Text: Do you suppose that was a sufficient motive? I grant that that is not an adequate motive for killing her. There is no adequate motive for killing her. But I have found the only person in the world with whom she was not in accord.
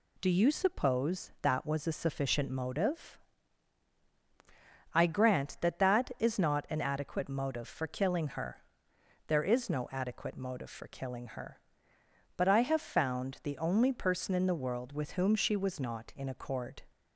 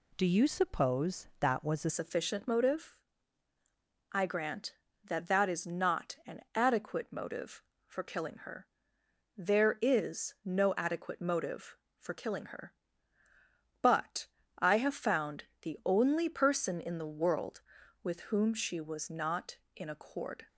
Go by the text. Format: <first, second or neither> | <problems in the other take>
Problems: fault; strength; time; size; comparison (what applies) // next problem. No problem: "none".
first | changes voice at "sufficient"; from 1.9 s on; 18.5 s long // pauses between "an" and "adequate"; slight; at 6.3 s; 0.16 s long // pauses between "But" and "I"; slight; at 14.2 s; 0.28 s long // pauses between "found" and "the"; slight; at 15.4 s; 0.18 s long